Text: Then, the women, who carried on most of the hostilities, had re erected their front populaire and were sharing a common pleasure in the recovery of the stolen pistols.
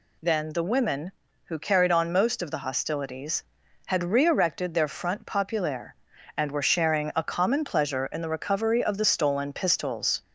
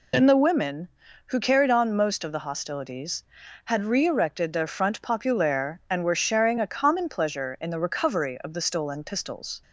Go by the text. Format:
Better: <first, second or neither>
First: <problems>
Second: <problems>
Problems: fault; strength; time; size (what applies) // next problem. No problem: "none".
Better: first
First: none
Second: loses the start of "Then"; at 0.1 s; 50 ms